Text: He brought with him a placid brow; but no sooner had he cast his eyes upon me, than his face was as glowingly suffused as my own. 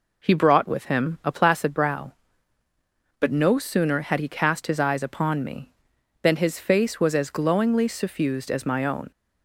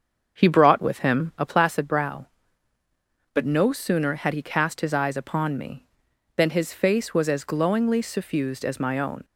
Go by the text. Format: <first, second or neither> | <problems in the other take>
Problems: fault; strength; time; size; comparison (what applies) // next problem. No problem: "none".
first | starts louder than the rest; until 1.4 s; 6.5 dB